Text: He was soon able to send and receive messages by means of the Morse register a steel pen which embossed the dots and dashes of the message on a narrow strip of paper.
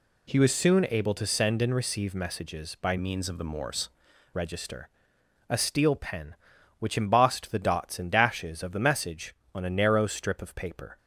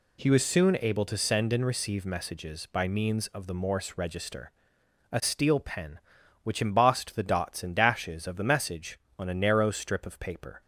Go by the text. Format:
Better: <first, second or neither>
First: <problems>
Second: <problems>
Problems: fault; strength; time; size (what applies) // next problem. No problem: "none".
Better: second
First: changes voice from "means" to "Morse"; from 2.9 to 3.8 s; 0.9 s long // pauses between "register" and "a"; noticeable; at 4.8 s; 0.62 s long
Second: pauses between "register" and "a"; noticeable; at 4.5 s; 0.62 s long